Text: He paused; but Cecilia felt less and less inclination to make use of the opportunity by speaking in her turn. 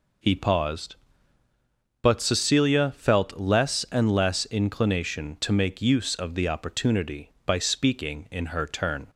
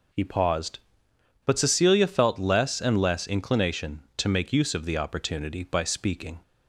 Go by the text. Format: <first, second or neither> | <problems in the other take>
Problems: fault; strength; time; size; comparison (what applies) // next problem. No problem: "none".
first | stops before "in her turn"; at 6.4 s